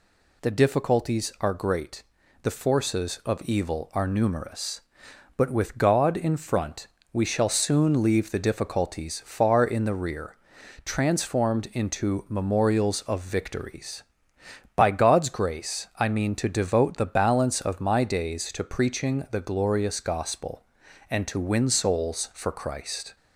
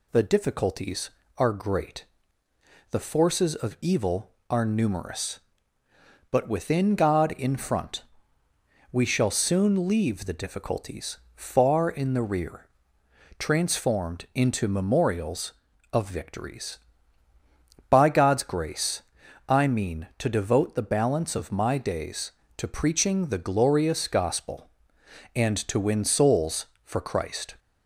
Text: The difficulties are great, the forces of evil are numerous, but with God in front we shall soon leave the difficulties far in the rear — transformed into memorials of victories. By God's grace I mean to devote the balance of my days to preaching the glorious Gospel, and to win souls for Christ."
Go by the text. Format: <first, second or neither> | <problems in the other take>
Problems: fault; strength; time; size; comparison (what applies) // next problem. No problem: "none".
first | says "within" for "with"; at 6.4 s // pauses between "front" and "we"; noticeable; at 8.0 s; 0.86 s long; slight in the first // pauses between "difficulties" and "far"; slight; at 11.1 s; 0.16 s long // pauses between "grace" and "I"; at 19.0 s; 0.44 s long